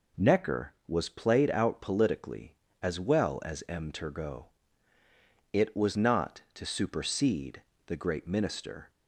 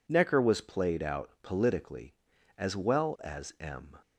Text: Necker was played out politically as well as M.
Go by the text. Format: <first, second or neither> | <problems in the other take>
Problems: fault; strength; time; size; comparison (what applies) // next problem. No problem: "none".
second | goes on to say "Turgot It was not to supersede the great minister"; strong; from 3.8 s on; 5.0 s long